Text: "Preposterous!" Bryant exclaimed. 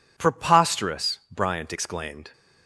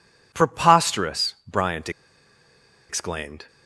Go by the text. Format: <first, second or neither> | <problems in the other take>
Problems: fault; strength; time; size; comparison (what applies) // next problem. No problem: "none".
first | pauses between "Bryant" and "exclaimed"; at 1.9 s; 0.99 s long